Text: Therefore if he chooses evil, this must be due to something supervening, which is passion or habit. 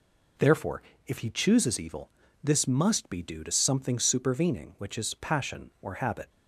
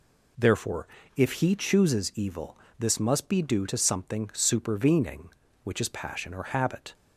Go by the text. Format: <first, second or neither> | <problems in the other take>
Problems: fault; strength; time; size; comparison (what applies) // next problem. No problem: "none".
neither | pauses between "Therefore" and "if"; slight; the same in both